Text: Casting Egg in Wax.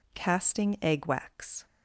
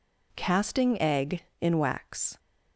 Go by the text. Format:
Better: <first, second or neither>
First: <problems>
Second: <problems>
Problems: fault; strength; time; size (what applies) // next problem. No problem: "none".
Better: second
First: skips "in"; at 1.0 s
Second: none